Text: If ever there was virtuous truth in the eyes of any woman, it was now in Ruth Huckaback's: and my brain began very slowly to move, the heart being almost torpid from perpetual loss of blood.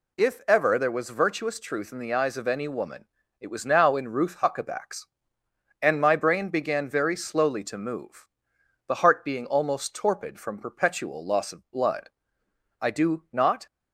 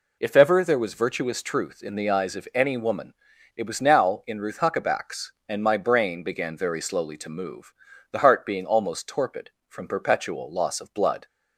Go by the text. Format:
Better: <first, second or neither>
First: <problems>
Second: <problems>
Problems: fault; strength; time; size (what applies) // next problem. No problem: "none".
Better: second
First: goes on to say "I do not"; noticeable; from 12.8 s on; 0.86 s long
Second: none